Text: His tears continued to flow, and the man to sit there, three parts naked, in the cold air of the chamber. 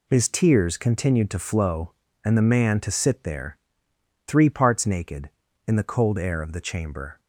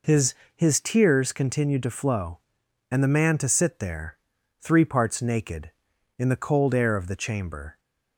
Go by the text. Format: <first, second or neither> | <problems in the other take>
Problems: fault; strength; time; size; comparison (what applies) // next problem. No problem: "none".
first | says "His" twice; at 0.5 s